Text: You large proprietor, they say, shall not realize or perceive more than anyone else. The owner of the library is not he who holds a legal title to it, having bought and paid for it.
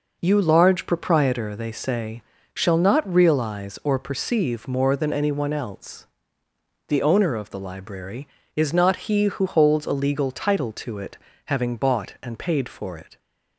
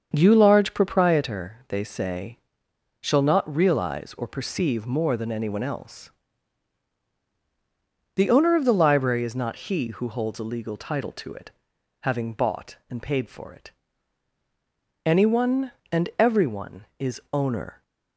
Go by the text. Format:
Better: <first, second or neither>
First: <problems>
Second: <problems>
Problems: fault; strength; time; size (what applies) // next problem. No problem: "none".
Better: first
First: none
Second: starts louder than the rest; until 1.1 s; 7 dB // goes on to say "Anyone and everyone is owner"; strong; from 15.0 s on; 2.7 s long